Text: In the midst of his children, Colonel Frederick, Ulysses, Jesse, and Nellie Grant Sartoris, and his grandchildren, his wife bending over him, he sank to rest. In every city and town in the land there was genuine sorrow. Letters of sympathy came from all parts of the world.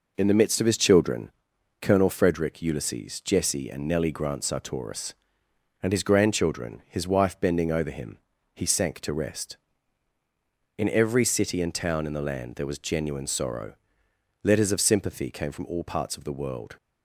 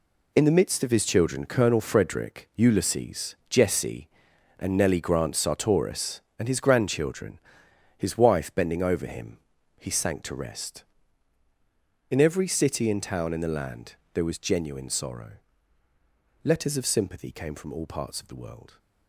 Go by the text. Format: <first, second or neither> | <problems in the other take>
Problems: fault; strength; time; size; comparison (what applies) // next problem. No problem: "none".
first | gets quieter; strong; throughout; 9.5 dB // pauses between "land" and "there"; slight; at 13.9 s; 0.18 s long